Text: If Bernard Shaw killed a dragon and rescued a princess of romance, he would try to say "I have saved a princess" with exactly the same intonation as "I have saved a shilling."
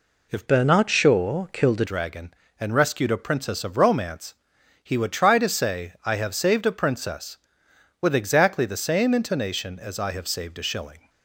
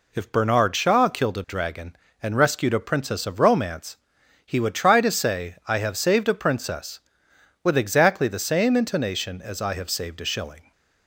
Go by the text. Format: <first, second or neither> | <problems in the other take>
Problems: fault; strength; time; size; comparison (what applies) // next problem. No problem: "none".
second | changes voice from "Bernard" to "a"; from 0.4 to 1.8 s; 1.4 s long